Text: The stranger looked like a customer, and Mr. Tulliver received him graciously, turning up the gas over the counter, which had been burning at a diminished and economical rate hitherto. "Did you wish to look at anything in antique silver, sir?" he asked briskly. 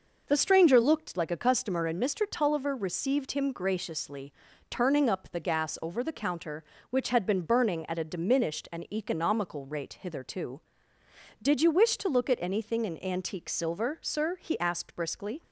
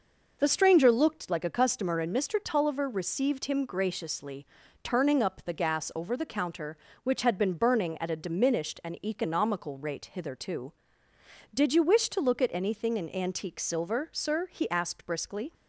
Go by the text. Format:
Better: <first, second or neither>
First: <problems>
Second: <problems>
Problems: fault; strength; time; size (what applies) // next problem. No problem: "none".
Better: neither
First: none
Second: none